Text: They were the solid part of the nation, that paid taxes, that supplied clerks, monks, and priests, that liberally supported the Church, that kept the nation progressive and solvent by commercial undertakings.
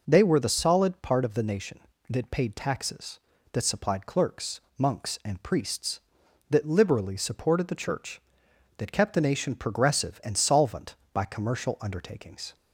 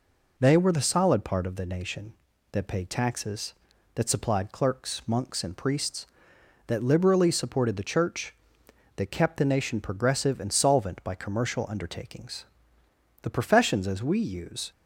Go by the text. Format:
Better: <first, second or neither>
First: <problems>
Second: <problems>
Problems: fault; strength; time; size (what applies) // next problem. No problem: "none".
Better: first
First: none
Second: goes on to say "The professions as we use"; from 13.2 s on; 1.5 s long